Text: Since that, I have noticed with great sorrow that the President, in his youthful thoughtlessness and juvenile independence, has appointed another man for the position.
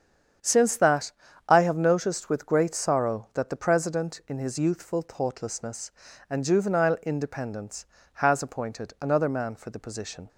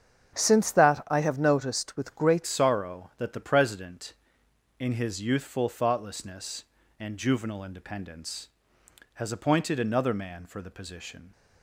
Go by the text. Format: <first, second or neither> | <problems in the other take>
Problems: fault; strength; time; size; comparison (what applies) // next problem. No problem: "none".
first | starts louder than the rest; strong; until 1.3 s; 7.5 dB; strong in the first // changes voice at "sorrow"; from 2.4 s on; 8.9 s long